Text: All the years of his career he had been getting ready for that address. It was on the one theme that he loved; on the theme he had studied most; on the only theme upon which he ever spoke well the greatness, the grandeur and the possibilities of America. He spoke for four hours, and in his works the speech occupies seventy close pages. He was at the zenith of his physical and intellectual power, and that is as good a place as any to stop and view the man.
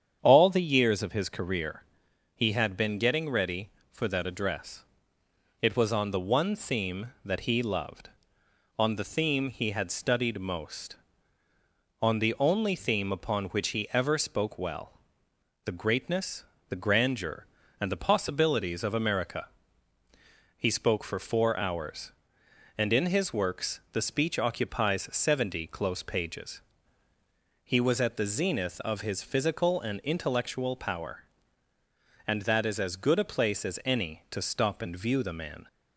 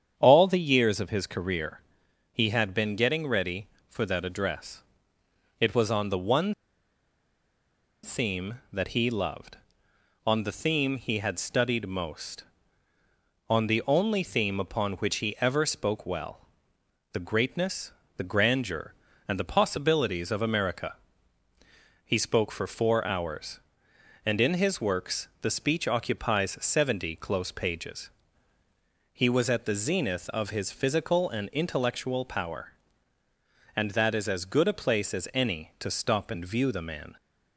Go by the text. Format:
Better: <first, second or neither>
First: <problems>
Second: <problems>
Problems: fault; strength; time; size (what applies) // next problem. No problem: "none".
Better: first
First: starts louder than the rest; strong; until 1.2 s; 8 dB // pauses between "career" and "he"; noticeable; at 1.8 s; 0.52 s long // pauses between "well" and "the"; noticeable; at 14.9 s; 0.66 s long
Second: starts louder than the rest; strong; until 1.1 s; 8 dB // pauses between "career" and "he"; noticeable; at 1.8 s; 0.52 s long // pauses between "one" and "theme"; strong; at 6.5 s; 1.5 s long // pauses between "well" and "the"; noticeable; at 16.4 s; 0.66 s long // pauses between "works" and "the"; slight; at 25.2 s; 0.16 s long